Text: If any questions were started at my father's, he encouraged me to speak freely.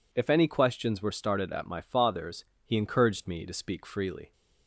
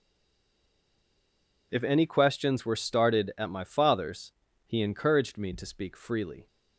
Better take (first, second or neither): first